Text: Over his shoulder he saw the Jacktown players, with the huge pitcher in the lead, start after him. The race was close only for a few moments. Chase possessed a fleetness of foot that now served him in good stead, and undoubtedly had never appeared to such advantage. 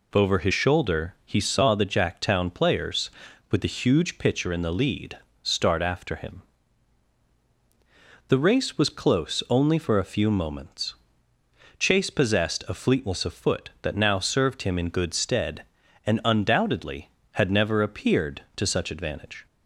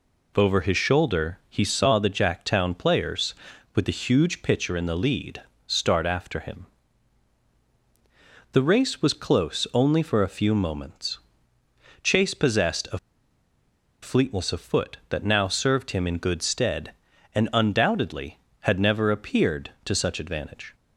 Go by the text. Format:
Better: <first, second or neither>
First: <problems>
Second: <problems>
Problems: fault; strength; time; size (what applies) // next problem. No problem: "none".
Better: first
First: none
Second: pauses between "a" and "fleetness"; at 12.9 s; 1.0 s long